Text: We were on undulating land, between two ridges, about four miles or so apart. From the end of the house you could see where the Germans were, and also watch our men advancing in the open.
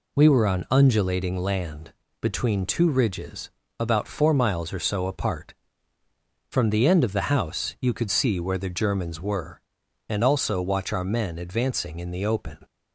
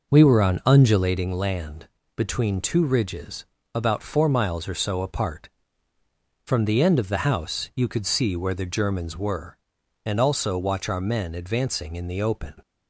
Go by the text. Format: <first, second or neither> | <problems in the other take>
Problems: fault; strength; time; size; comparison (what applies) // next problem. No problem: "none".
first | starts louder than the rest; noticeable; until 1.3 s; 5 dB